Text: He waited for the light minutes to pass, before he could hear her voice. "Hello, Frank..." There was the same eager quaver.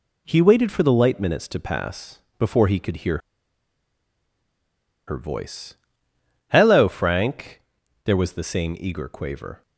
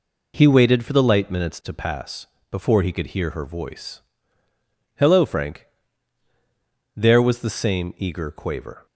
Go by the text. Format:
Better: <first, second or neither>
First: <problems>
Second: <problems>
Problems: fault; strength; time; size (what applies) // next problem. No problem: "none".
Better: second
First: pauses between "hear" and "her"; strong; at 3.1 s; 1.8 s long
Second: none